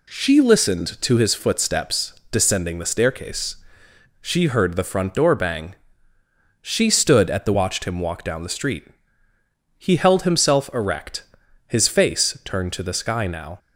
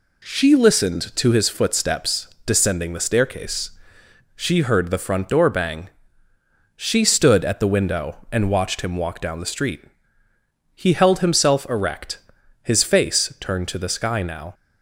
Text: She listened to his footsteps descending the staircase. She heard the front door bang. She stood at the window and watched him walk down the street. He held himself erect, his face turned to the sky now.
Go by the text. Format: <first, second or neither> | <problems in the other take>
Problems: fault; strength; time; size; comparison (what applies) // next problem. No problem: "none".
second | pauses between "footsteps" and "descending"; slight; at 2.1 s; 0.16 s long; slight in the second // skips "window and"; at 7.5 s